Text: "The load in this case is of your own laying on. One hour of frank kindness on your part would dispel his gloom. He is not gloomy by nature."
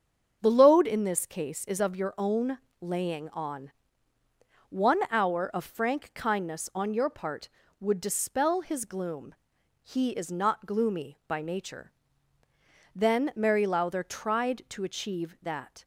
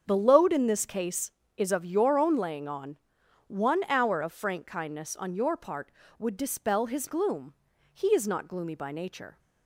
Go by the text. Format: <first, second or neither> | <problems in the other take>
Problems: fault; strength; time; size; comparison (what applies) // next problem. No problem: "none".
second | starts louder than the rest; until 1.4 s; 7 dB; strong in the second // pauses between "own" and "laying"; slight; at 2.5 s; 0.24 s long // goes on to say "Then Mary Lowther tried to achieve that"; strong; from 12.9 s on; 2.9 s long